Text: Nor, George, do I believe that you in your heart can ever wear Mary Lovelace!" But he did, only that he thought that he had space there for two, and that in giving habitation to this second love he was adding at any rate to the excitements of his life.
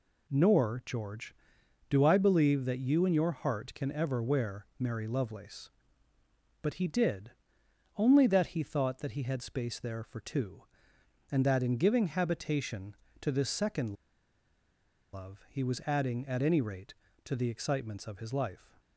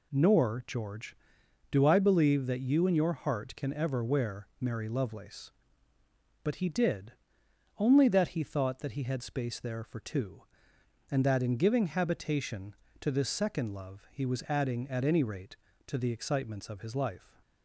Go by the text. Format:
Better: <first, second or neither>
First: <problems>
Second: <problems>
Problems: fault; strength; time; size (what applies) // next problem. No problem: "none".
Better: second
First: pauses between "second" and "love"; at 13.9 s; 1.1 s long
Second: none